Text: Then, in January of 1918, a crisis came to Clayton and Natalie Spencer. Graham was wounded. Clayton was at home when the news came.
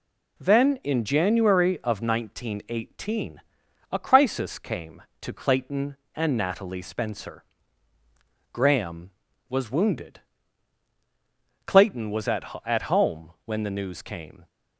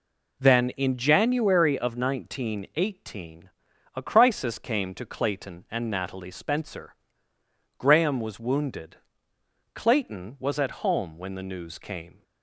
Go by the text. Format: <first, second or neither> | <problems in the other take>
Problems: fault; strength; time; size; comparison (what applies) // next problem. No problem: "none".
second | says "at" twice; at 12.6 s // pauses between "home" and "when"; slight; at 13.3 s; 0.16 s long